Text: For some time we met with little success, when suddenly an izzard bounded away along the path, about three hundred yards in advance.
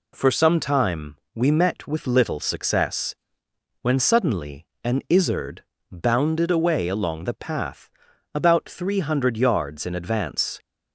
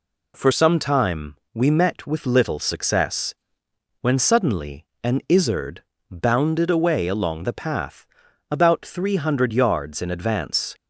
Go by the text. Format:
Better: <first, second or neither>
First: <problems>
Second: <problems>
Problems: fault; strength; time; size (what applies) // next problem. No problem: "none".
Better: neither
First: pauses between "time" and "we"; slight; at 1.1 s; 0.18 s long // pauses between "suddenly" and "an"; slight; at 4.6 s; 0.20 s long // pauses between "izzard" and "bounded"; slight; at 5.6 s; 0.26 s long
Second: pauses between "time" and "we"; slight; at 1.3 s; 0.18 s long // pauses between "suddenly" and "an"; slight; at 4.8 s; 0.20 s long // pauses between "izzard" and "bounded"; slight; at 5.8 s; 0.26 s long